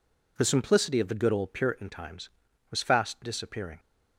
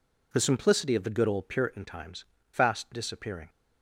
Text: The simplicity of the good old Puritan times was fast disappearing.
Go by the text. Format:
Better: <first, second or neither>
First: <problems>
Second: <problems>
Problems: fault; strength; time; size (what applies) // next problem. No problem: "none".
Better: first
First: none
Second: skips "was"; at 2.3 s